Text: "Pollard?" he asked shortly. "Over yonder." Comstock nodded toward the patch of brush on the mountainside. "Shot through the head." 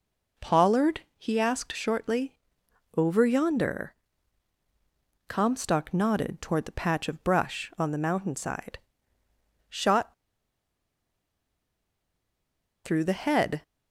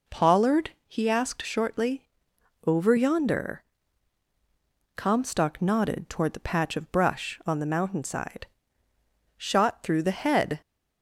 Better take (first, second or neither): second